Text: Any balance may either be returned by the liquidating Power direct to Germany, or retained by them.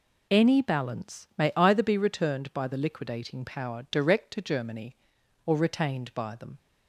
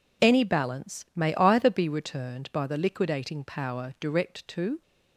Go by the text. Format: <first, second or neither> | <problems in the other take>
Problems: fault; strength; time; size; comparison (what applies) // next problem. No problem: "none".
first | stops before "Germany or retained by them"; at 4.8 s